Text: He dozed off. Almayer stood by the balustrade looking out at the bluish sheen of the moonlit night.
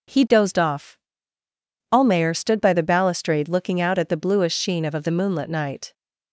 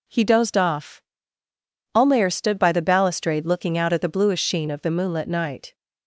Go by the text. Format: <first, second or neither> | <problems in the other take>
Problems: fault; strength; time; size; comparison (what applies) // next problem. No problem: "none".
second | says "of" twice; at 4.9 s